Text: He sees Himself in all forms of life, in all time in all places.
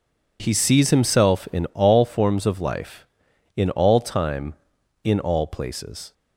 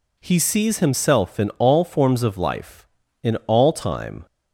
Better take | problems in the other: first | stops before "in all places"; at 4.2 s

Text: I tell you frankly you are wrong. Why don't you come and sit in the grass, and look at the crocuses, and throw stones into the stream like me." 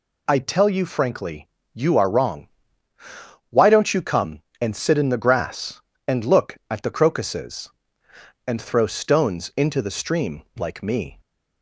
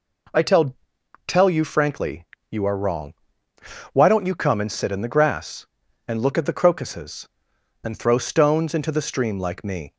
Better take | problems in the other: first | says "tell" twice; at 1.2 s // pauses between "frankly" and "you"; slight; at 2.2 s; 0.24 s long; slight in the first

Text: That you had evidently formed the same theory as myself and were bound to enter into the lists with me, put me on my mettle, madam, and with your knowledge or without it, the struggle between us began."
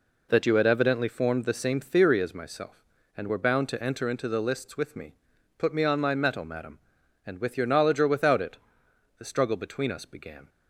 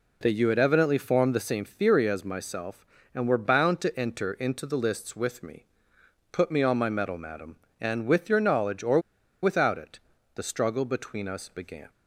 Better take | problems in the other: first | pauses between "or" and "without"; at 8.9 s; 0.42 s long

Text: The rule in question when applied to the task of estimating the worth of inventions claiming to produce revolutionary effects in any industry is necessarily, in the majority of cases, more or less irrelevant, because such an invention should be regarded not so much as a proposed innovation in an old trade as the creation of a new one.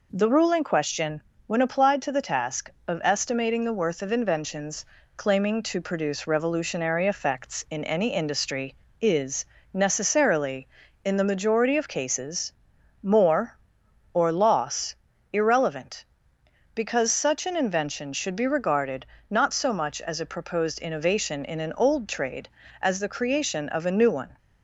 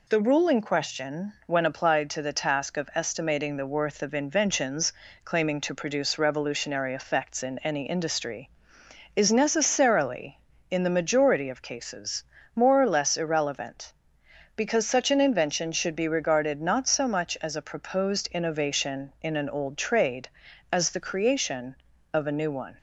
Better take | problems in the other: second | pauses between "question" and "when"; slight; at 1.2 s; 0.24 s long // pauses between "inventions" and "claiming"; slight; at 4.8 s; 0.30 s long; slight in the second // pauses between "is" and "necessarily"; slight; at 9.4 s; 0.28 s long // says "loss" for "less"; at 14.3 s // pauses between "regarded" and "not"; slight; at 19.0 s; 0.24 s long

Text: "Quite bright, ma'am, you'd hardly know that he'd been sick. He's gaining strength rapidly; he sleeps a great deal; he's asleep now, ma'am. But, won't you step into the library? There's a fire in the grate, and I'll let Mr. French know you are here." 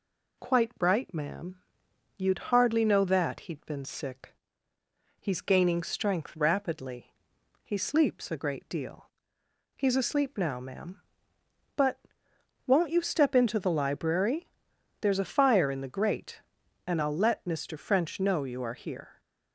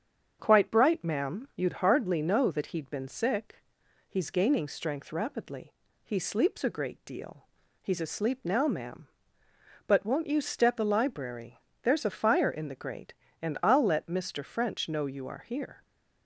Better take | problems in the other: first | starts louder than the rest; strong; until 1.4 s; 7.5 dB // skips "into"; at 10.7 s

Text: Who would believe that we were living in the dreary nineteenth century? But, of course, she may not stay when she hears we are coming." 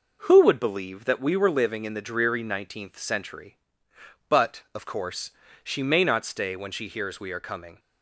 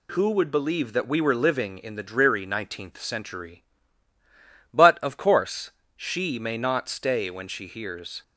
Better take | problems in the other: first | stops before "we are coming"; at 8.2 s

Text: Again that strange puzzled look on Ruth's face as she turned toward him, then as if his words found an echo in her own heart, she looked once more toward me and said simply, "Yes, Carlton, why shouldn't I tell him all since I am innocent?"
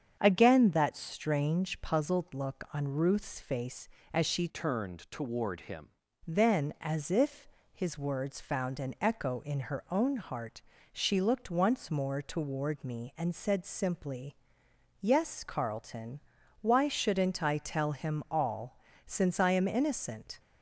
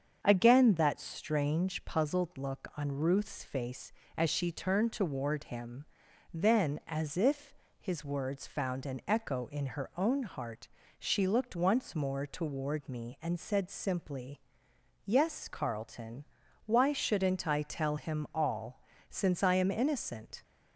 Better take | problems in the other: second | starts louder than the rest; strong; until 1.2 s; 7.5 dB; also in the second // changes voice from "turned" to "him"; from 4.4 to 5.8 s; 1.4 s long // pauses between "if" and "his"; slight; at 7.4 s; 0.26 s long; slight in the second // pauses between "all" and "since"; slight; at 18.7 s; 0.28 s long; slight in the second

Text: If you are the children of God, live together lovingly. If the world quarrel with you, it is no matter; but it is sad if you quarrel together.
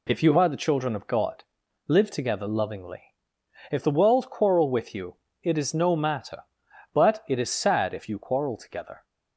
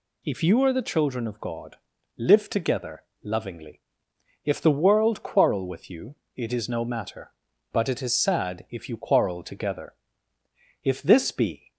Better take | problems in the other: first | pauses between "together" and "lovingly"; slight; at 3.0 s; 0.22 s long // goes on to say "If this be"; noticeable; from 10.8 s on; 0.86 s long

